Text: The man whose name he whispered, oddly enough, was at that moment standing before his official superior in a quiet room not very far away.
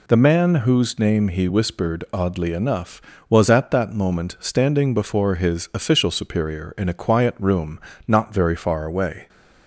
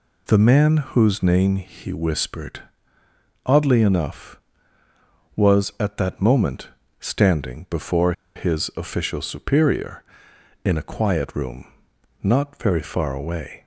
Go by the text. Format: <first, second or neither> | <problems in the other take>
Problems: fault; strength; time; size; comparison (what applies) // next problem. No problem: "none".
first | pauses between "moment" and "standing"; slight; at 6.6 s; 0.32 s long // pauses between "before" and "his"; slight; at 8.1 s; 0.23 s long // pauses between "room" and "not"; noticeable; at 11.6 s; 0.56 s long; slight in the first